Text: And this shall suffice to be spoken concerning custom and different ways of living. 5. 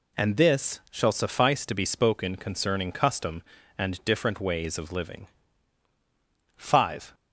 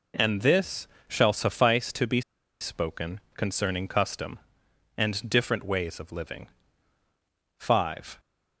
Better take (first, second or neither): first